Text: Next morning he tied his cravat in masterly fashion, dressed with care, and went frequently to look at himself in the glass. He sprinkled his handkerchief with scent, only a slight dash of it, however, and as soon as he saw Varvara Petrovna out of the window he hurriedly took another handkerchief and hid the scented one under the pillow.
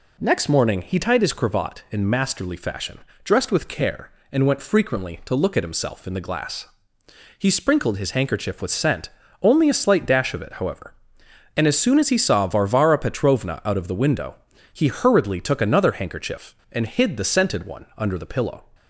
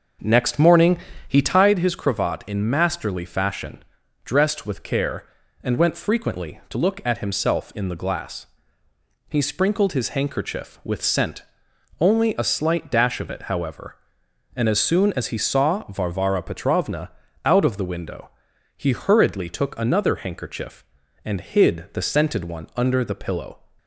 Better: first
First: pauses between "window" and "he"; at 14.3 s; 0.40 s long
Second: starts louder than the rest; noticeable; until 1.8 s; 6 dB // pauses between "morning" and "he"; slight; at 0.9 s; 0.30 s long // pauses between "Petrovna" and "out"; slight; at 17.1 s; 0.34 s long // pauses between "window" and "he"; noticeable; at 18.2 s; 0.50 s long

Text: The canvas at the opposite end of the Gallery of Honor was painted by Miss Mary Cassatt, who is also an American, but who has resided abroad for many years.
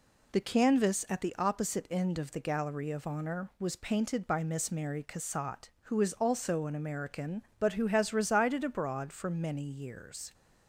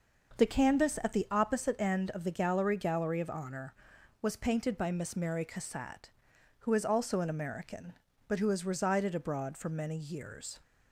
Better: first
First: none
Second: starts louder than the rest; noticeable; until 1.4 s; 6 dB // says "Gallery" twice; at 2.7 s

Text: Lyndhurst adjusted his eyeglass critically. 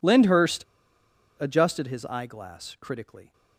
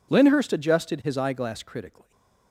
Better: second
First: pauses between "Lyndhurst" and "adjusted"; noticeable; at 0.6 s; 0.74 s long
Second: none

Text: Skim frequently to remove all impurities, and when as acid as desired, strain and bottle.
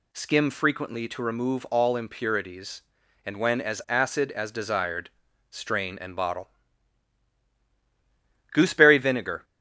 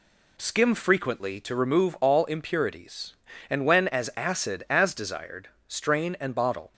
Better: second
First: goes on to say "Gooseberry vinegar"; noticeable; from 8.5 s on; 0.92 s long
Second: none

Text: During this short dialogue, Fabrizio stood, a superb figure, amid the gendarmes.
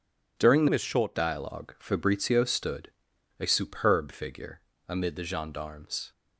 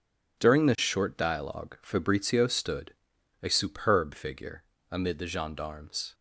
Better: second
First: changes voice from "this" to "short"; from 0.6 to 1.1 s; 0.5 s long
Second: none

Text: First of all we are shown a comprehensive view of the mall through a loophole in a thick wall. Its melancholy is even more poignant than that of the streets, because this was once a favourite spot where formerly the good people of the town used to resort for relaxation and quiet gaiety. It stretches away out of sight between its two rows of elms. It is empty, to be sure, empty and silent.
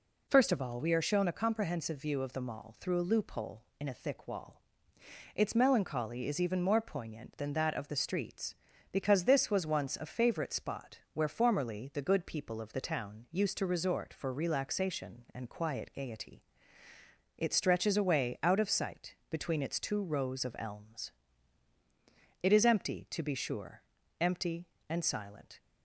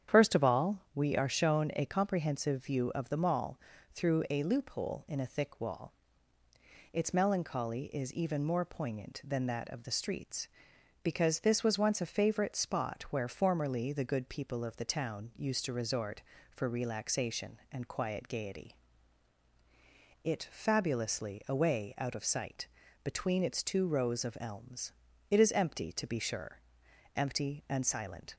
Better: first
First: none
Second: starts louder than the rest; strong; until 1.2 s; 9 dB // pauses between "mall" and "through"; slight; at 3.5 s; 0.34 s long // says "fabulously" for "stretches"; at 20.4 s // pauses between "sight" and "between"; at 22.6 s; 0.38 s long

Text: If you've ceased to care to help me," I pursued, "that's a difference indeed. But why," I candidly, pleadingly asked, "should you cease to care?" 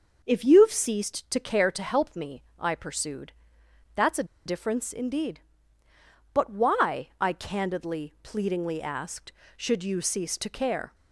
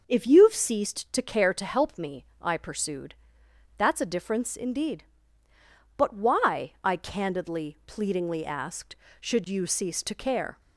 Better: second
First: starts louder than the rest; noticeable; until 1.2 s; 6 dB // pauses between "a" and "difference"; slight; at 4.2 s; 0.21 s long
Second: starts louder than the rest; noticeable; until 1.0 s; 6 dB

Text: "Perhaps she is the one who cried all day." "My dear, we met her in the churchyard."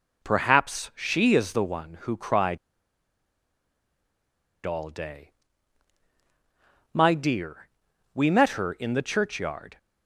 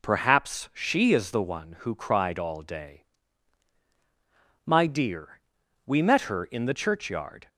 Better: second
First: pauses between "cried" and "all"; strong; at 2.5 s; 2.0 s long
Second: none

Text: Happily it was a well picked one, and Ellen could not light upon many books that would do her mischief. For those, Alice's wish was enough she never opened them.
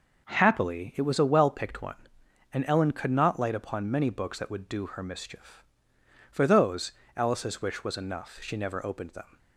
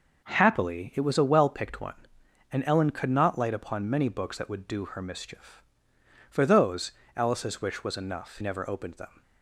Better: first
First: none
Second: skips "she"; at 8.3 s

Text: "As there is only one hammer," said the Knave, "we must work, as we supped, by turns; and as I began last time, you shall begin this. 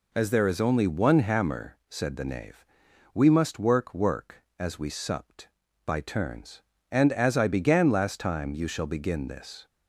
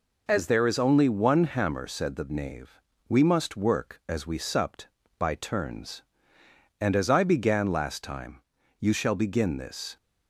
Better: second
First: says "work" twice; at 3.9 s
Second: none

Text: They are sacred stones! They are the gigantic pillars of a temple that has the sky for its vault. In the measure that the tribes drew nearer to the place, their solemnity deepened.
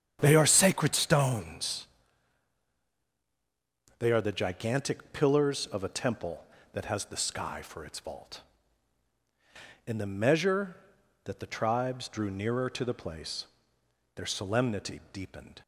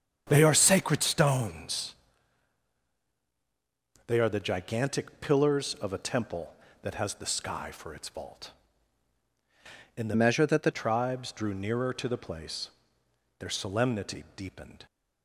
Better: first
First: starts louder than the rest; strong; until 1.2 s; 8.5 dB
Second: starts louder than the rest; strong; until 1.2 s; 8 dB // changes voice from "measure" to "the"; from 10.1 to 10.6 s; 0.5 s long

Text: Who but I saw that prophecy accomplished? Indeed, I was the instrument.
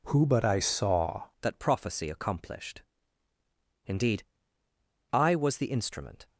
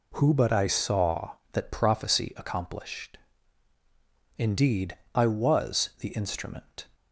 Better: second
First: changes voice at "that"; from 1.4 s on; 4.8 s long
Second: none

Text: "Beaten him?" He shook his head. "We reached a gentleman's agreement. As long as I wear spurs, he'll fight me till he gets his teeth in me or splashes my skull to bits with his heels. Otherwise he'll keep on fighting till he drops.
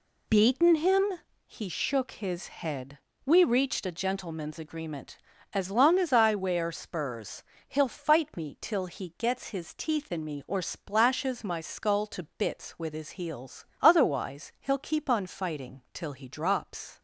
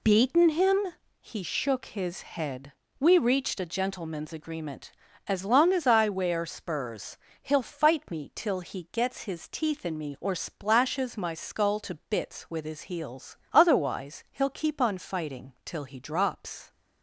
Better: neither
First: pauses between "to" and "bits"; slight; at 12.2 s; 0.16 s long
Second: pauses between "to" and "bits"; slight; at 11.9 s; 0.16 s long

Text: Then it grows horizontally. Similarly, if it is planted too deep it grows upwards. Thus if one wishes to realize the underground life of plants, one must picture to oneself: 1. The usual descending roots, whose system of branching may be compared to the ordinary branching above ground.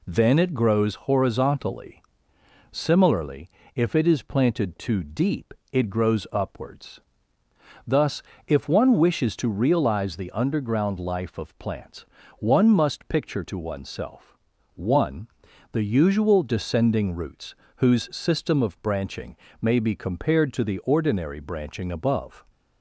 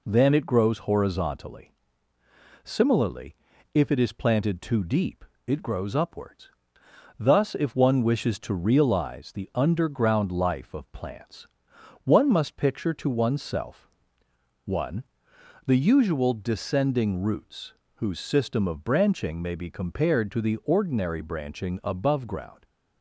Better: second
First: pauses between "deep" and "it"; slight; at 5.5 s; 0.18 s long // pauses between "Thus" and "if"; slight; at 8.2 s; 0.26 s long // pauses between "branching" and "may"; slight; at 19.3 s; 0.24 s long // stops before "ground"; at 22.4 s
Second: pauses between "deep" and "it"; slight; at 5.2 s; 0.22 s long

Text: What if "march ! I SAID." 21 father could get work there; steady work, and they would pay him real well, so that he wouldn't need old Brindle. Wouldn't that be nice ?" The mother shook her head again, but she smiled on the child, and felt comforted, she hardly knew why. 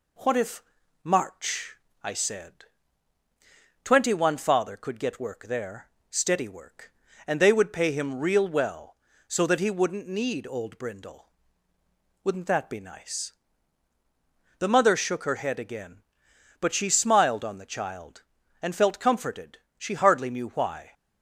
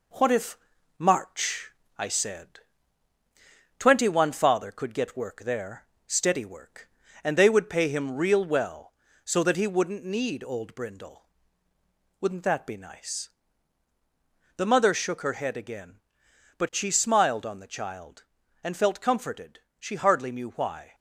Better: first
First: pauses between "if" and "march"; at 0.6 s; 0.42 s long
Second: gets quieter; noticeable; throughout; 6 dB // pauses between "if" and "march"; at 0.5 s; 0.42 s long

